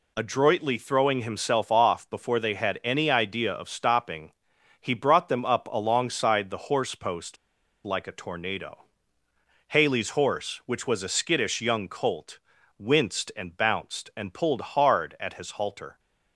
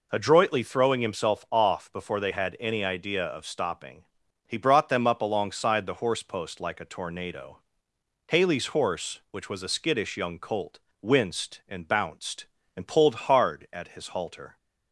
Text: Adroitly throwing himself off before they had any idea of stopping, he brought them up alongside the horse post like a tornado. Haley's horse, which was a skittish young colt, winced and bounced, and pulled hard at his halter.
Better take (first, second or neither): second